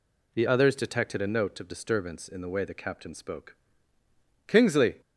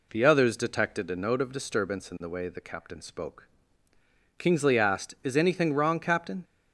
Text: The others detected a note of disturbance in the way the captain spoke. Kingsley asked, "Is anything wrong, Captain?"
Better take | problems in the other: second | stops before "asked Is anything wrong Captain"; at 5.0 s

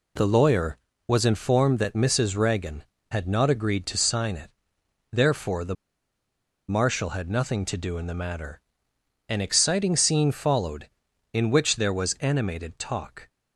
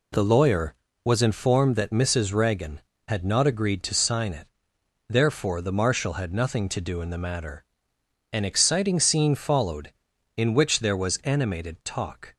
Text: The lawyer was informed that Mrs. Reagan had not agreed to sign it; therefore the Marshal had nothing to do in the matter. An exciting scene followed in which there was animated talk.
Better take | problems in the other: second | pauses between "the" and "Marshal"; noticeable; at 5.7 s; 0.94 s long

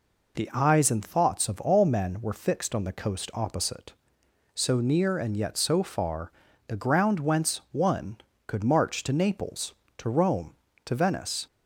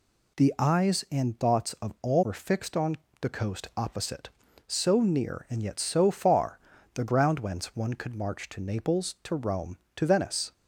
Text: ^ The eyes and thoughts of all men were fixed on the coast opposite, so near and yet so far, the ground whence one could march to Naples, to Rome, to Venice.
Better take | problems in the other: first | skips "men"; at 2.2 s // pauses between "on" and "the"; slight; at 2.9 s; 0.26 s long

